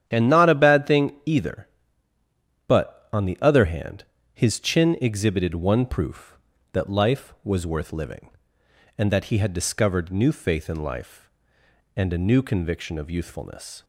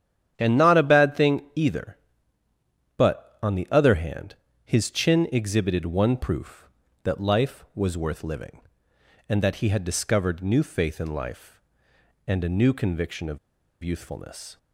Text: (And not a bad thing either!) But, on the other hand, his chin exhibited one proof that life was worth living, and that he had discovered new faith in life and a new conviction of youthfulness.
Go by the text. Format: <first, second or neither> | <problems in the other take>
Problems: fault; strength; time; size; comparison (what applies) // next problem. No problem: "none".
first | starts louder than the rest; strong; until 1.3 s; 9.5 dB; strong in the first // pauses between "of" and "youthfulness"; at 13.3 s; 0.44 s long